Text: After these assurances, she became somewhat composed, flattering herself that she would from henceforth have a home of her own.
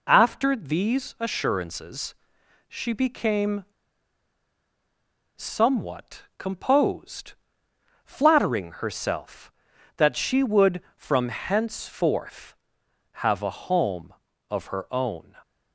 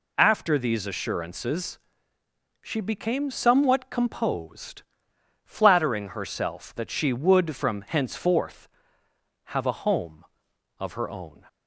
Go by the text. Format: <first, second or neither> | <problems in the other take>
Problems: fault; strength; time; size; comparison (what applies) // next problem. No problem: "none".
second | pauses between "became" and "somewhat"; strong; at 3.6 s; 1.7 s long